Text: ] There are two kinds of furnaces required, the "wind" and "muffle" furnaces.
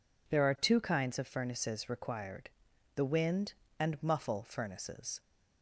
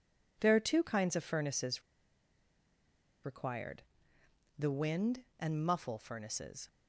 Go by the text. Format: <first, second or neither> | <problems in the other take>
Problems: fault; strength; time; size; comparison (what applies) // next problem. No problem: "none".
first | pauses between "furnaces" and "required"; strong; at 1.8 s; 1.4 s long